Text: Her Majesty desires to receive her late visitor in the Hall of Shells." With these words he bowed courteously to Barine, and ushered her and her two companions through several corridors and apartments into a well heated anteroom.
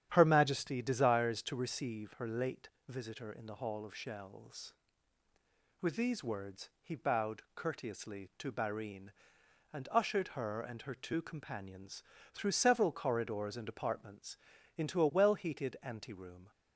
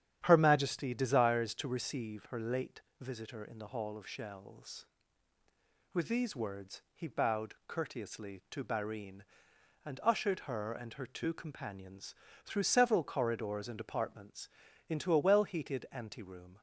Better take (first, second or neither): neither